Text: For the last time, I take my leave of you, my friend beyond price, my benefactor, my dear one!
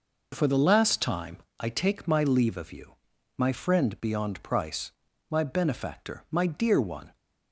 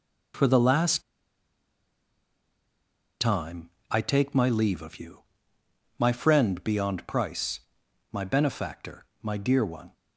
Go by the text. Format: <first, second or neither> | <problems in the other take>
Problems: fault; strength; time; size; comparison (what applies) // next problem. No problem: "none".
first | pauses between "last" and "time"; strong; at 1.0 s; 2.1 s long